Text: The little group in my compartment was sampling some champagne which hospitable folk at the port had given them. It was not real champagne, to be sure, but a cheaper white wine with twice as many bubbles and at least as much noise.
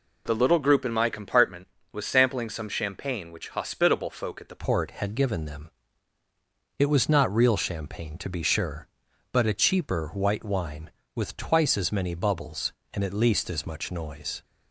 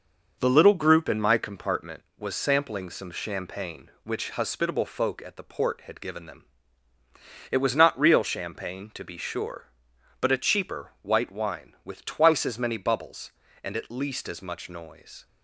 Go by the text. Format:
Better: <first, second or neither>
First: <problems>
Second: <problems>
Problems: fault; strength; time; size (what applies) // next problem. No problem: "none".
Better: second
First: changes voice at "port"; from 4.5 s on; 9.9 s long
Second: none